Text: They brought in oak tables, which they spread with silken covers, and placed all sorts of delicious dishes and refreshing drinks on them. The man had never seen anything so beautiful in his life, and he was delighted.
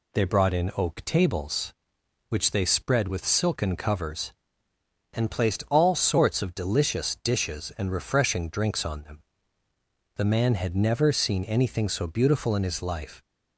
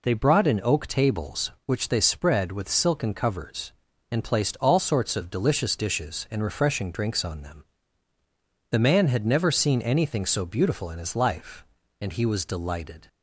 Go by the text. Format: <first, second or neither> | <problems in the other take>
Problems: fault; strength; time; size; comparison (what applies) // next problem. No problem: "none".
second | stops before "and he was delighted"; at 13.2 s